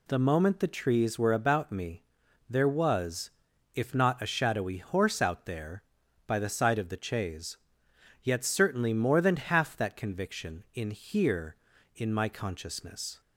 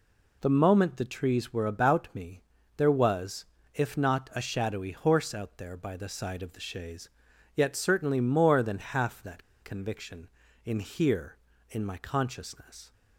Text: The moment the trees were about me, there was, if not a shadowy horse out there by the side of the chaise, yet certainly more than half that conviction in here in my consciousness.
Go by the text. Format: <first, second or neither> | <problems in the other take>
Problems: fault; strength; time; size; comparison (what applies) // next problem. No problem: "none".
first | pauses between "that" and "conviction"; slight; at 9.4 s; 0.21 s long